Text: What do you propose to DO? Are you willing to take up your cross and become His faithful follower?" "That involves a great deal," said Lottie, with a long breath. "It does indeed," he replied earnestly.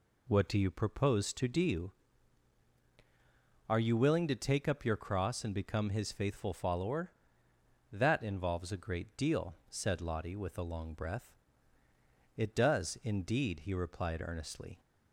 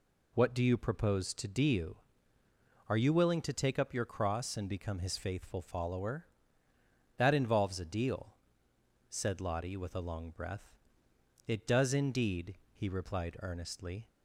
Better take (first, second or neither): first